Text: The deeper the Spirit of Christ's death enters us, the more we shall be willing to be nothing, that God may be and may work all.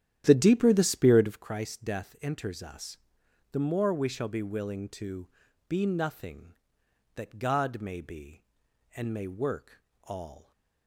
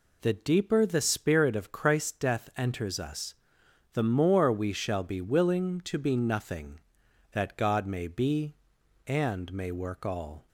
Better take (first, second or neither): second